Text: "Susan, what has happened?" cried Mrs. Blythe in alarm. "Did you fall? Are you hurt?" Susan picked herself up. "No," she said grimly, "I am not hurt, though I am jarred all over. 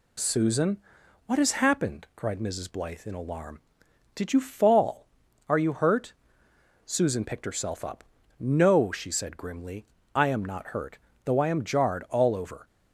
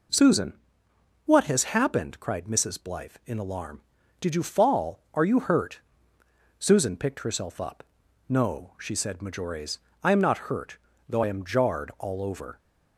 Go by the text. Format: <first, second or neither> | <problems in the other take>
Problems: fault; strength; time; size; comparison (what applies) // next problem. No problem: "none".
first | says "majores" for "grimly"; at 9.2 s